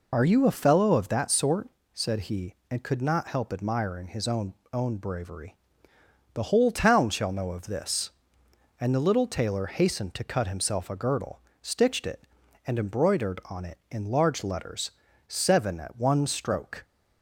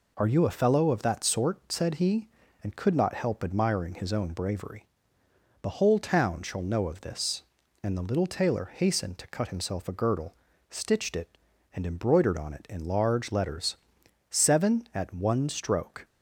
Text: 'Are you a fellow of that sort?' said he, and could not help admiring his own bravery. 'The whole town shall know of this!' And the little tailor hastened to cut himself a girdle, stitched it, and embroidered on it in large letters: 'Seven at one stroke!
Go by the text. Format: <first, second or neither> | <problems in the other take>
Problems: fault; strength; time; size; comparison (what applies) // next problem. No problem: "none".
second | says "own" twice; at 4.7 s